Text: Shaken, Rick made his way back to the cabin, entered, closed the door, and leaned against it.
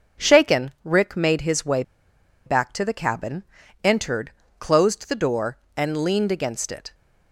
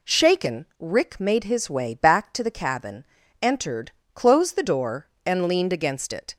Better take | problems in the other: second | pauses between "way" and "back"; noticeable; at 1.8 s; 0.63 s long

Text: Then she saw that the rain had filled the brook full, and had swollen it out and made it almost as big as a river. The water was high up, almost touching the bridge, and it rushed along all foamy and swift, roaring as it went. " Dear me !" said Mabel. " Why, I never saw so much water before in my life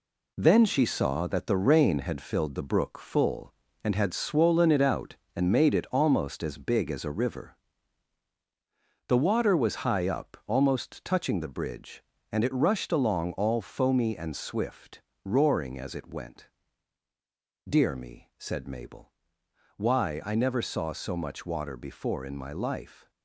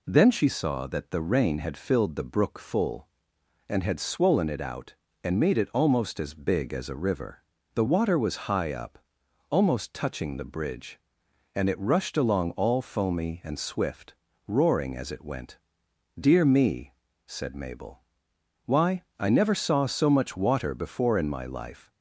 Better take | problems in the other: second | gets quieter; strong; throughout; 14 dB

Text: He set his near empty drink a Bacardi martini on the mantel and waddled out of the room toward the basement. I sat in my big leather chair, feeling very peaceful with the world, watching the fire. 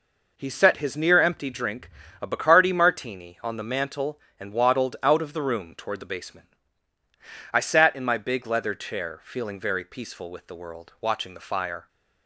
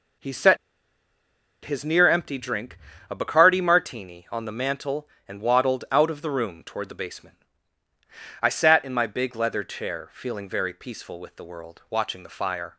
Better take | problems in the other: first | pauses between "set" and "his"; at 0.5 s; 1.0 s long // pauses between "drink" and "a"; slight; at 2.7 s; 0.32 s long; slight in the first

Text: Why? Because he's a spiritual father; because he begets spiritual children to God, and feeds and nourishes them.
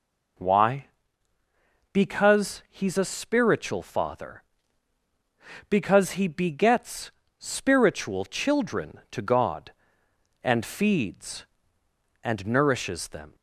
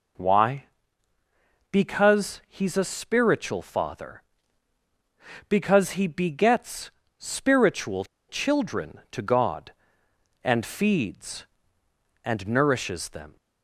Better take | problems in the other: first | pauses between "begets" and "spiritual"; slight; at 6.8 s; 0.30 s long; slight in the first // pauses between "spiritual" and "children"; slight; at 8.0 s; 0.23 s long

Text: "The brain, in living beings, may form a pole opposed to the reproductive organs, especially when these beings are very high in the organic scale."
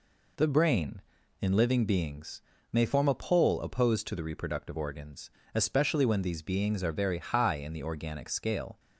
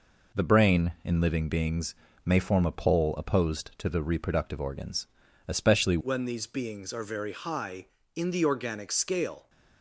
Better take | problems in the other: first | changes voice at "when"; from 6.0 s on; 3.4 s long

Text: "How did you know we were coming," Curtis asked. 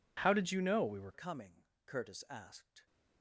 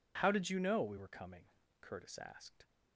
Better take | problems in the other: second | changes voice at "coming"; from 1.1 s on; 1.7 s long

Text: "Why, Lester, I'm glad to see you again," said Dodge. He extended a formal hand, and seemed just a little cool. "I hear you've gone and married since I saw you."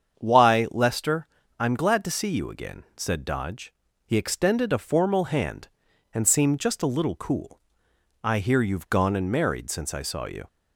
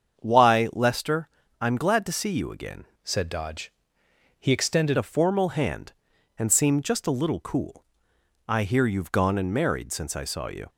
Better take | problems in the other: first | starts louder than the rest; strong; until 1.2 s; 7 dB; strong in the first // changes voice from "said" to "extended"; from 3.0 to 4.9 s; 1.9 s long

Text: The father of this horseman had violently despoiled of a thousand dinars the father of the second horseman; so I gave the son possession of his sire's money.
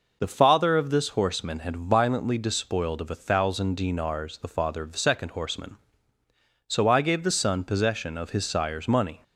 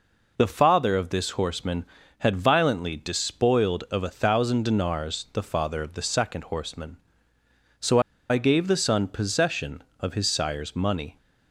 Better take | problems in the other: first | pauses between "so" and "I"; slight; at 7.9 s; 0.30 s long

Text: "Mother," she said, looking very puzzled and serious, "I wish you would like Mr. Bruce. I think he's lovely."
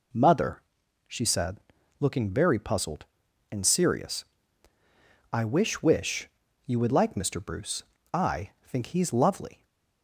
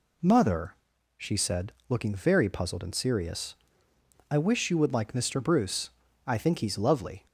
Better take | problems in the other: second | says "wish" twice; at 5.8 s // pauses between "I" and "think"; slight; at 8.4 s; 0.16 s long

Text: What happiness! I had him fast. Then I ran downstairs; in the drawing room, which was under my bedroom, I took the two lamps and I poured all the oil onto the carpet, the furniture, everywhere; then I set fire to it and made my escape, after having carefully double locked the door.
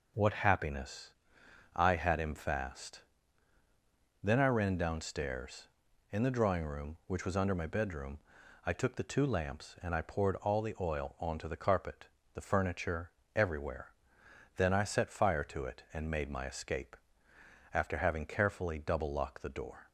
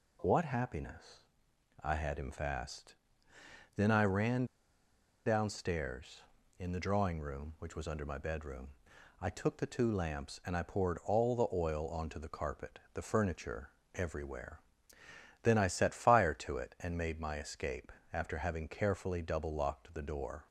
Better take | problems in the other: first | pauses between "ran" and "downstairs"; noticeable; at 4.4 s; 0.81 s long

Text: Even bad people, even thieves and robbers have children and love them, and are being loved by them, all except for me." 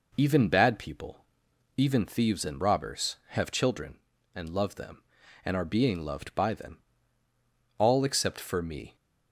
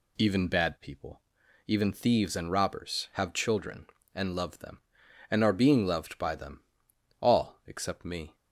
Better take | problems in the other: first | skips "for"; at 8.0 s

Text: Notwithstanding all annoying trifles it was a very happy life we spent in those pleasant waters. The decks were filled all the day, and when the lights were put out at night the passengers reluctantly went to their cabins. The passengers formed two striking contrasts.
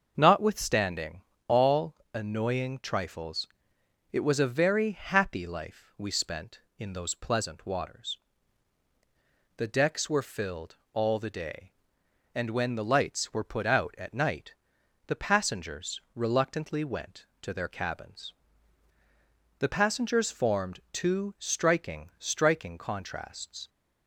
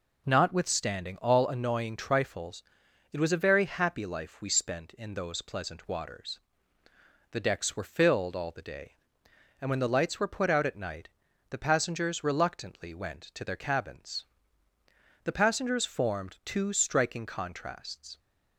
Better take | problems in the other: second | starts louder than the rest; until 1.1 s; 6.5 dB // pauses between "Notwithstanding" and "all"; slight; at 1.2 s; 0.26 s long // pauses between "all" and "annoying"; slight; at 1.9 s; 0.18 s long // pauses between "trifles" and "it"; noticeable; at 3.4 s; 0.64 s long; noticeable in the second // pauses between "filled" and "all"; slight; at 10.7 s; 0.18 s long // pauses between "night" and "the"; noticeable; at 14.5 s; 0.54 s long; also in the second // says "striking" twice; at 22.1 s

